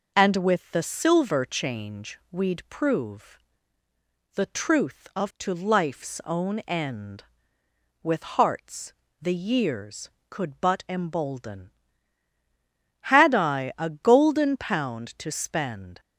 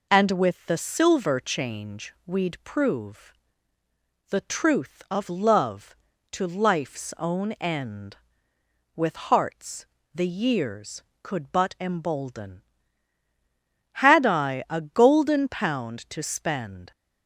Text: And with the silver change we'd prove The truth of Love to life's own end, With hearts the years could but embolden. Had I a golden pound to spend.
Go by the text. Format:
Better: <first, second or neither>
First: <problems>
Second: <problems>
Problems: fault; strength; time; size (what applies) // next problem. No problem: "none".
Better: second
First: pauses between "prove" and "The"; noticeable; at 3.3 s; 0.98 s long // skips "Love"; at 5.3 s // pauses between "hearts" and "the"; slight; at 8.9 s; 0.30 s long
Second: pauses between "prove" and "The"; noticeable; at 3.3 s; 0.98 s long // pauses between "hearts" and "the"; slight; at 9.8 s; 0.30 s long